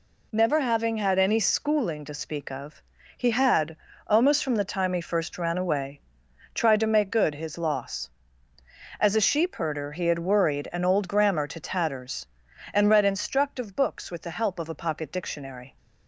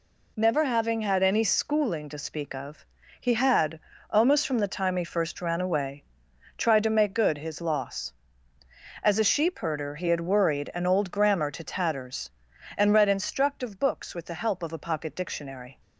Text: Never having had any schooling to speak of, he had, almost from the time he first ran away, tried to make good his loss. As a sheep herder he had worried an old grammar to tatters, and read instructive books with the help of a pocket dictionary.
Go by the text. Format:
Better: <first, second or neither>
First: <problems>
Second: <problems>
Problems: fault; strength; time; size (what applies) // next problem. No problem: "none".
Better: neither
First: none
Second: none